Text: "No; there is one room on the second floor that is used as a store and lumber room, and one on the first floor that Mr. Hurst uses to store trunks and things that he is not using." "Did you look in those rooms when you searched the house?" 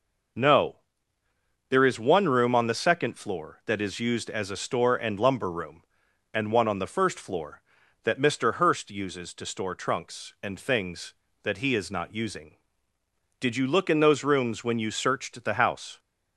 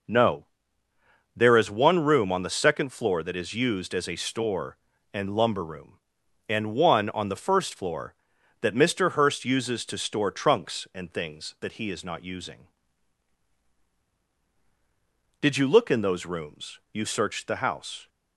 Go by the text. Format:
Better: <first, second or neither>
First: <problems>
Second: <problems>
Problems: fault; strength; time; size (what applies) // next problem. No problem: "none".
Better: first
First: none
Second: skips "when"; at 16.8 s